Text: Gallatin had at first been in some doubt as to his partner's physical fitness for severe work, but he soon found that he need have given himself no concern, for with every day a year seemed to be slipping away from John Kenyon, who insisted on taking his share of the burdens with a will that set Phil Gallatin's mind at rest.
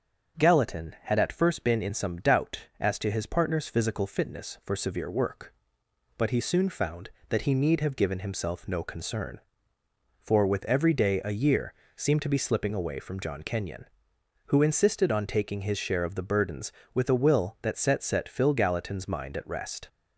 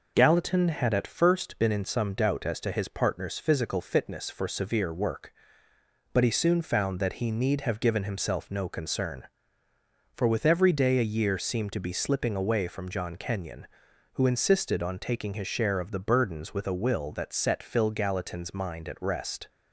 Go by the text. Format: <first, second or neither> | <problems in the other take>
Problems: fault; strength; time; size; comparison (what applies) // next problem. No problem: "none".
second | starts louder than the rest; strong; until 1.4 s; 7 dB // pauses between "year" and "seemed"; slight; at 11.7 s; 0.22 s long // says "set" twice; at 18.0 s